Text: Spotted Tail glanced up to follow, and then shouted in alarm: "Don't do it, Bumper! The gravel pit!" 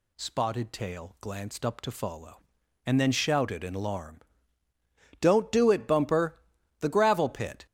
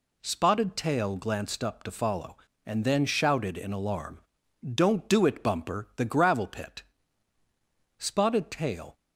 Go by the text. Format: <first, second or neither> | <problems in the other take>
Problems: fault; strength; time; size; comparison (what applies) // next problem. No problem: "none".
first | goes on to say "Spotted Tail"; noticeable; from 7.9 s on; 1.0 s long